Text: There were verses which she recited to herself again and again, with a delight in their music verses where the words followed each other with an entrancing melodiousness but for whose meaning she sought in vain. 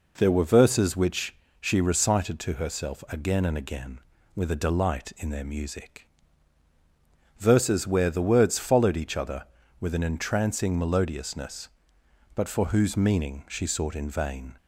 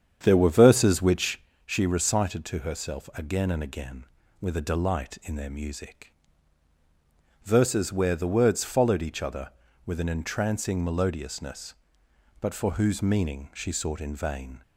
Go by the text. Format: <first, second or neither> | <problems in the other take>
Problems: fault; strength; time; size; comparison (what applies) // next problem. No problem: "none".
first | starts louder than the rest; strong; until 1.5 s; 8 dB // pauses between "which" and "she"; slight; at 1.3 s; 0.26 s long; slight in the first // pauses between "music" and "verses"; strong; at 6.1 s; 1.3 s long; strong in the first